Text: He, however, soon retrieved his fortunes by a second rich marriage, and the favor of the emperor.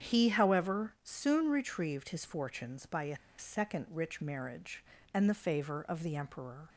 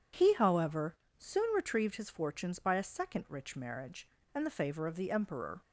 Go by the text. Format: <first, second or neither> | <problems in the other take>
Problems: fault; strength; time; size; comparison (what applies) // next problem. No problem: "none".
second | starts louder than the rest; strong; until 1.1 s; 8.5 dB // pauses between "a" and "second"; slight; at 3.1 s; 0.21 s long